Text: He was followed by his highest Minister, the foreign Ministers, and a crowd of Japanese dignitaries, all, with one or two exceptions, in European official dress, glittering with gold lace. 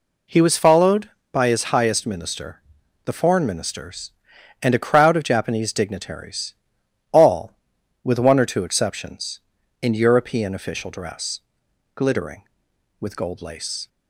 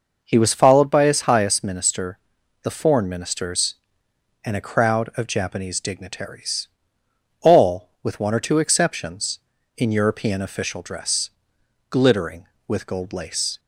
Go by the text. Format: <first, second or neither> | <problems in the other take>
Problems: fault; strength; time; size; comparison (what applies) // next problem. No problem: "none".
neither | none